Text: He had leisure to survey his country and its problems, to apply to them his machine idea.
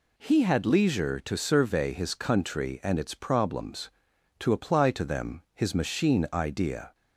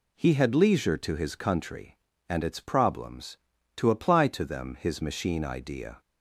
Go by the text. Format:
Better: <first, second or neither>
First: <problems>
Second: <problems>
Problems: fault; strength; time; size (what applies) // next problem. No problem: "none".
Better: first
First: none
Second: skips "survey"; at 1.1 s